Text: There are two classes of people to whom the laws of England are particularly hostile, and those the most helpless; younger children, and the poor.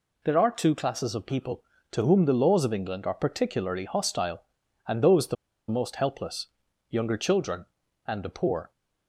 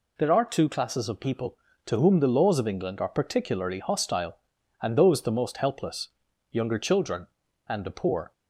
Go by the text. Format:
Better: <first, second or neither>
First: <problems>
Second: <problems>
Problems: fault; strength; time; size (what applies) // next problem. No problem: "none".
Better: second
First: pauses between "the" and "most"; slight; at 5.3 s; 0.33 s long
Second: none